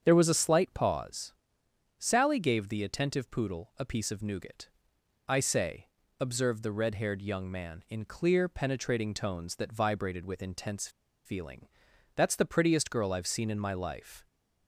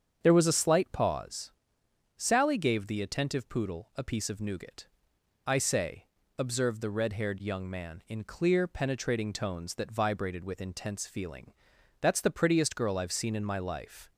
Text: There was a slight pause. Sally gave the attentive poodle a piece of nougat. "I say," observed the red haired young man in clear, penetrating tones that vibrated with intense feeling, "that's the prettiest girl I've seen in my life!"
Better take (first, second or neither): second